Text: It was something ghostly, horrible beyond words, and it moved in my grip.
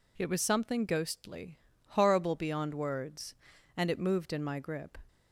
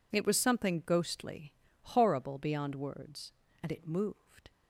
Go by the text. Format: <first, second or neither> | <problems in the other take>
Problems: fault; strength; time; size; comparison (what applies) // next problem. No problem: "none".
first | stops before "in my grip"; at 4.5 s